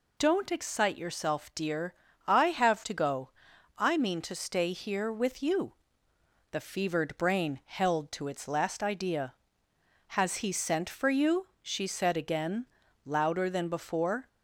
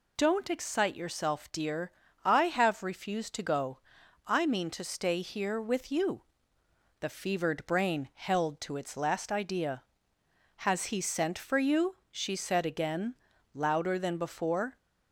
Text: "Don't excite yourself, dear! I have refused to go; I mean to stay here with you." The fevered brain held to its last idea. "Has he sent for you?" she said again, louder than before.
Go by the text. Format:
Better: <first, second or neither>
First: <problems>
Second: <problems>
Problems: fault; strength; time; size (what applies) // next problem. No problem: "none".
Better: second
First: skips "refused"; at 2.8 s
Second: none